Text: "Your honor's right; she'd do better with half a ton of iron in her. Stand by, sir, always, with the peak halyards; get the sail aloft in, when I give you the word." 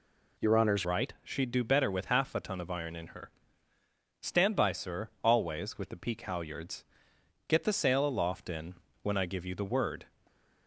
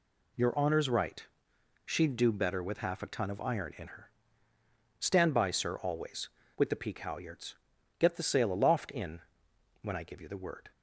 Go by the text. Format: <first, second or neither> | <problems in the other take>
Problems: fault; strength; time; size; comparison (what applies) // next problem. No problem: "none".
second | changes voice at "right"; from 0.8 s on; 9.2 s long // stays silent after the last word; slight; from 10.0 s on; 0.6 s long